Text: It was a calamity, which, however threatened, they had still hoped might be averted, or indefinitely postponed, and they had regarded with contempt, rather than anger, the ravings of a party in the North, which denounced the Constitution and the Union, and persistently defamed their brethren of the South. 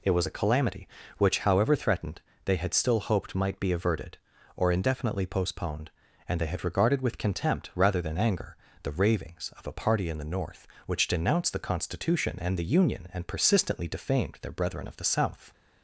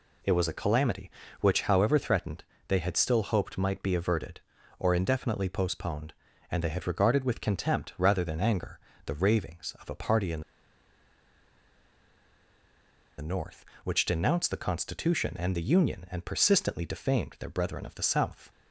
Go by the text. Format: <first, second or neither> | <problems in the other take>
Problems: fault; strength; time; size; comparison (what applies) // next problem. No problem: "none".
first | pauses between "in" and "the"; strong; at 10.4 s; 2.7 s long